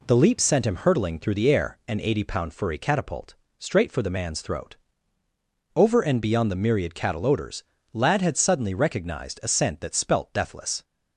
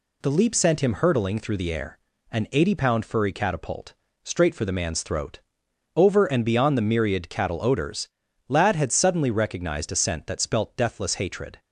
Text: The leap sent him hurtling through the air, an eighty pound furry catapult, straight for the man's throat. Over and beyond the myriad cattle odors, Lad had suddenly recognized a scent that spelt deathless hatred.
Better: second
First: stops before "hatred"; at 10.8 s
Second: none

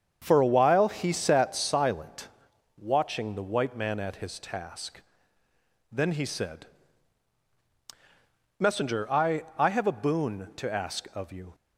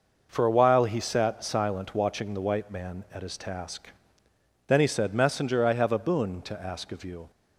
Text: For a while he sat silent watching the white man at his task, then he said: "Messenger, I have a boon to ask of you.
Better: second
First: starts louder than the rest; strong; until 1.2 s; 7.5 dB // pauses between "silent" and "watching"; noticeable; at 2.2 s; 0.48 s long // says "I" twice; at 9.5 s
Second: none

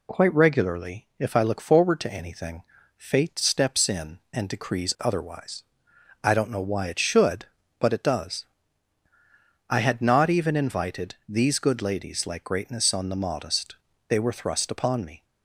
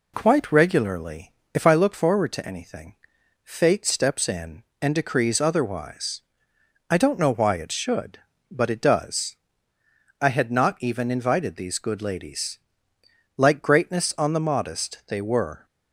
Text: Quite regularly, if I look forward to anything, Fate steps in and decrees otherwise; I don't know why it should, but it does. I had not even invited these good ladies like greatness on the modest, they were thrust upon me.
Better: first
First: none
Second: pauses between "ladies" and "like"; noticeable; at 12.5 s; 0.76 s long // stops before "thrust upon me"; at 15.6 s

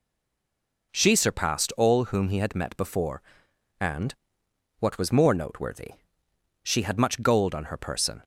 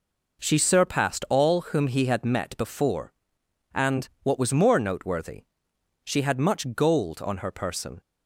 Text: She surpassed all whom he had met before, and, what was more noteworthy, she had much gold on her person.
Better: second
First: stays silent before the first word; slight; until 0.9 s; 0.9 s long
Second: none

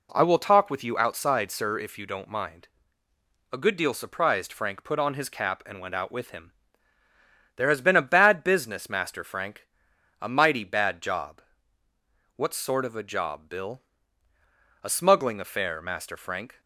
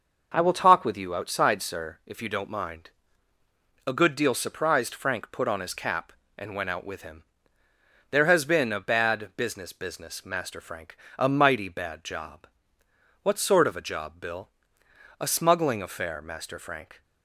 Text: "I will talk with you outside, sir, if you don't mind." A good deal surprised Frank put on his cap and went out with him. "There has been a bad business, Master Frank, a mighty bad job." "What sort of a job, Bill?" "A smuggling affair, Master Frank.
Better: first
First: none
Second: says "business" twice; at 9.7 s

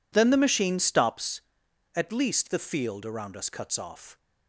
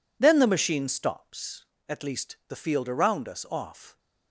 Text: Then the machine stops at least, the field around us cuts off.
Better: first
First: none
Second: skips "cuts"; at 3.4 s

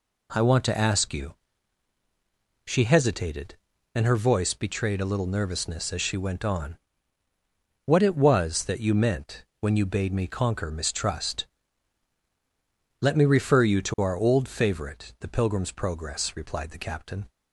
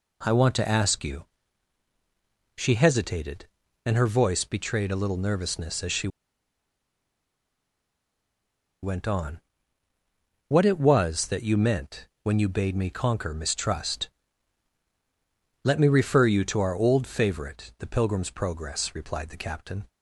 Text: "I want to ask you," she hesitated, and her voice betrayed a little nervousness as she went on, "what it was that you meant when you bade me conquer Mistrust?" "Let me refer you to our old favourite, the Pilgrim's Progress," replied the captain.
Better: first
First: pauses between "meant" and "when"; slight; at 9.4 s; 0.16 s long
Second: pauses between "she" and "went"; strong; at 6.0 s; 2.7 s long // pauses between "meant" and "when"; slight; at 12.0 s; 0.16 s long

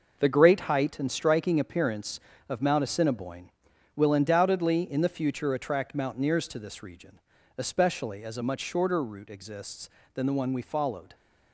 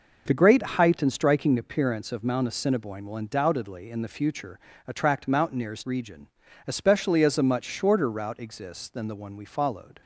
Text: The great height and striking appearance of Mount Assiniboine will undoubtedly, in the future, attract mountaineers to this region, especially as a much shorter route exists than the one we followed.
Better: first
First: none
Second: skips "to this"; at 5.8 s

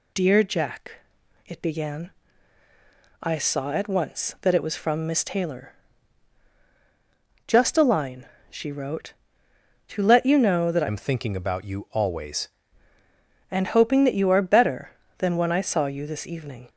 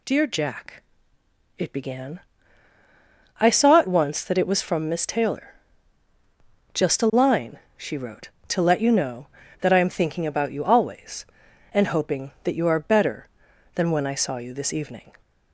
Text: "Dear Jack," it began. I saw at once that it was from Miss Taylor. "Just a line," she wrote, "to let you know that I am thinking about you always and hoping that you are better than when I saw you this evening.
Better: second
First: changes voice from "am" to "always"; from 10.8 to 12.4 s; 1.6 s long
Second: none

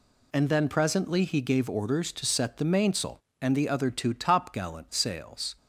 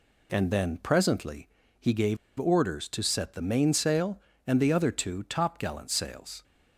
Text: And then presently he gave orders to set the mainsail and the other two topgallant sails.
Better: first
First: none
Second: pauses between "presently" and "he"; slight; at 1.4 s; 0.30 s long // pauses between "gave" and "orders"; slight; at 2.1 s; 0.22 s long

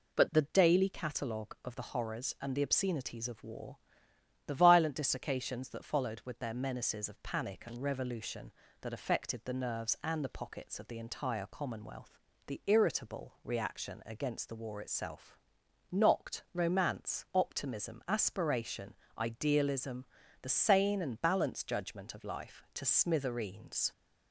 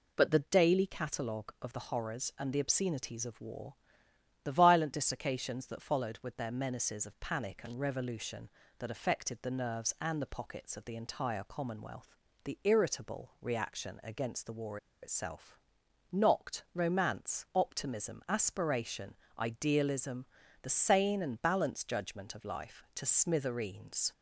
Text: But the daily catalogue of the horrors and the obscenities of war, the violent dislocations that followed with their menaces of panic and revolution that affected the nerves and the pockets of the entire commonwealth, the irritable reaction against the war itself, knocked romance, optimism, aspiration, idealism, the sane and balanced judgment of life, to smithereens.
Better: first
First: none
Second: pauses between "war" and "itself"; slight; at 14.7 s; 0.25 s long

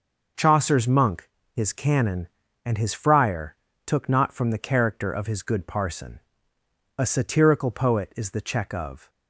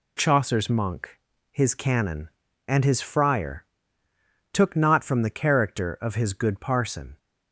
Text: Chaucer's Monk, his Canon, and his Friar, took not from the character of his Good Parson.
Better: second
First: goes on to say "A satirical poet is the check of"; strong; from 6.9 s on; 2.1 s long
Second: none

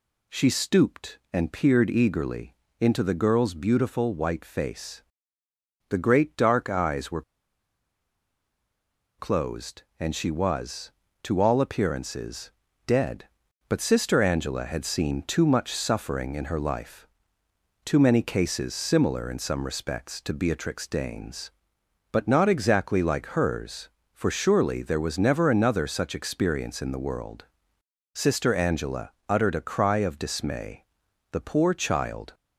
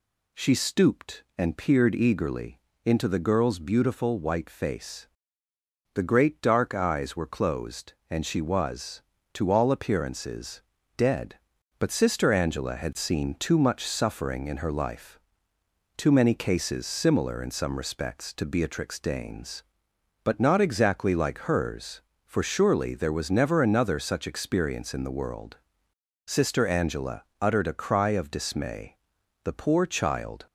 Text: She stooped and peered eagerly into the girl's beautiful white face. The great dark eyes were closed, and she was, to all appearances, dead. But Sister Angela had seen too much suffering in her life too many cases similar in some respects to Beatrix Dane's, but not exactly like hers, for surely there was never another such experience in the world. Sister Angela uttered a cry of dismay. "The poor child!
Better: second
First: pauses between "eagerly" and "into"; slight; at 2.5 s; 0.26 s long // pauses between "were" and "closed"; strong; at 7.2 s; 1.9 s long // pauses between "life" and "too"; noticeable; at 17.0 s; 0.78 s long // pauses between "Angela" and "uttered"; slight; at 29.1 s; 0.18 s long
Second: pauses between "eagerly" and "into"; slight; at 2.5 s; 0.26 s long // pauses between "life" and "too"; noticeable; at 15.1 s; 0.78 s long // pauses between "Angela" and "uttered"; slight; at 27.2 s; 0.18 s long

